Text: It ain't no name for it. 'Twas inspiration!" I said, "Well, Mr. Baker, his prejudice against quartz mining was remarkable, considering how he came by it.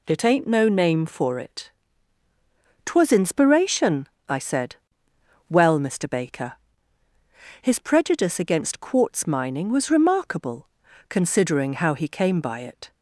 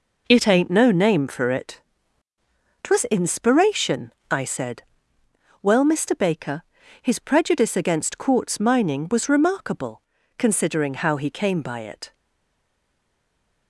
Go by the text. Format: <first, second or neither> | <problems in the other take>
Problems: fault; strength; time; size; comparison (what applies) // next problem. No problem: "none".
first | stays silent after the last word; noticeable; from 12.1 s on; 1.5 s long